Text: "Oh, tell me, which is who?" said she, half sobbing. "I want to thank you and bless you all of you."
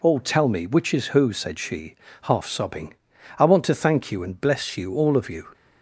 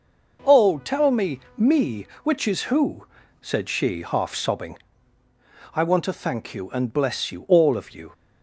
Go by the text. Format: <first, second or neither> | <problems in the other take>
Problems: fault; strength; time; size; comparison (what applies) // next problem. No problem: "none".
first | says "me" twice; at 1.5 s